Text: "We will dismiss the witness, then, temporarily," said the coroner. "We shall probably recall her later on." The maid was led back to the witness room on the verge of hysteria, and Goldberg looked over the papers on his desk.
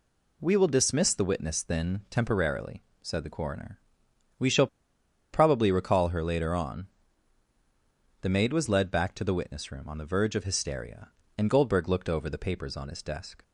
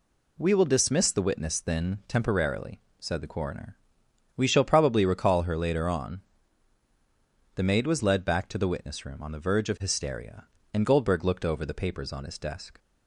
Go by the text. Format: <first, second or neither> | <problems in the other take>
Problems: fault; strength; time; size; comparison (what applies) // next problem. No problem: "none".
second | pauses between "shall" and "probably"; noticeable; at 4.6 s; 0.66 s long